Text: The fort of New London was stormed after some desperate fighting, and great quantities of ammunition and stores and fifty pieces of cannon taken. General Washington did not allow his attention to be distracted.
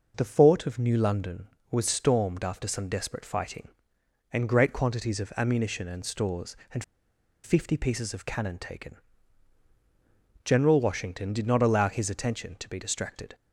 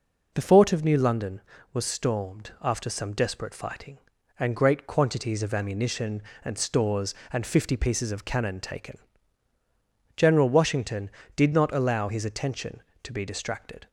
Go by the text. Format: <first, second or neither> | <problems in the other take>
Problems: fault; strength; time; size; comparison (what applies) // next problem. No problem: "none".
second | pauses between "and" and "fifty"; noticeable; at 6.8 s; 0.62 s long